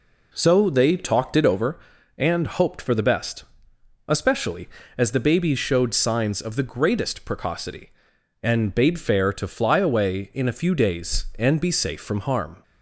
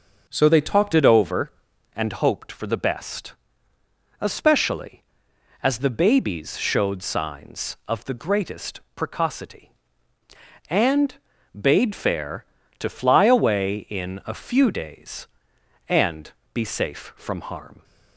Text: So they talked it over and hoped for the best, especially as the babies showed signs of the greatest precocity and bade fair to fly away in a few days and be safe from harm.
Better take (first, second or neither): first